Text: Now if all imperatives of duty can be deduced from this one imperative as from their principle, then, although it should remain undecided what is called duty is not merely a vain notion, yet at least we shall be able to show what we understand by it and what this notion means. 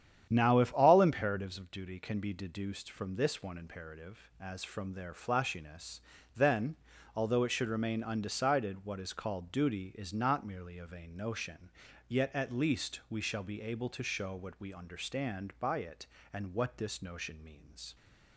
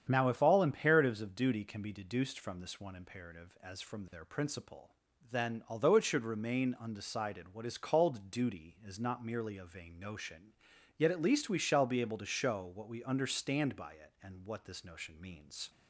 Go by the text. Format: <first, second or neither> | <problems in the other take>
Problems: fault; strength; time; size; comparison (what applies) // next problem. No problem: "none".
second | starts louder than the rest; strong; until 1.3 s; 9.5 dB; strong in the second // says "flashiness" for "principle"; at 5.1 s